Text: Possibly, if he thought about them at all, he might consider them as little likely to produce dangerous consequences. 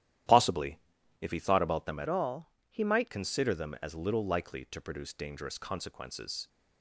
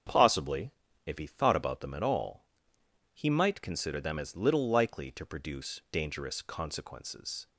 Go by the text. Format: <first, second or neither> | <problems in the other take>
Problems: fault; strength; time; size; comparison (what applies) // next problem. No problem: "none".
second | starts louder than the rest; strong; until 1.7 s; 12 dB; strong in the second // changes voice from "all" to "might"; from 2.0 to 3.1 s; 1.1 s long